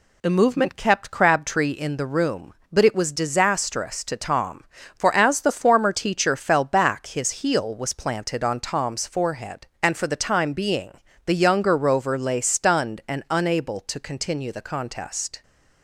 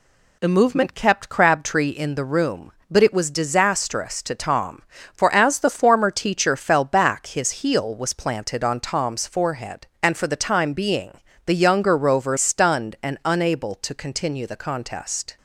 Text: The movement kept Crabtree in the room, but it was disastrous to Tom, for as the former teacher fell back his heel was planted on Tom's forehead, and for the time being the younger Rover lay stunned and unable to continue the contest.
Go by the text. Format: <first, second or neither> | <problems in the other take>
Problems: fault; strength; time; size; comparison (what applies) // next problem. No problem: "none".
first | pauses between "being" and "the"; slight; at 11.1 s; 0.36 s long; slight in the first // skips "lay"; at 12.3 s